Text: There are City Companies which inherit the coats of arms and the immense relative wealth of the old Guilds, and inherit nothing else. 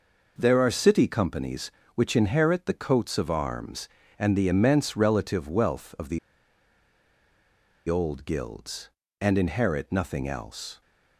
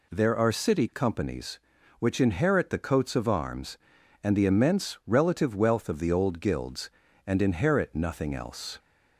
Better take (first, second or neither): second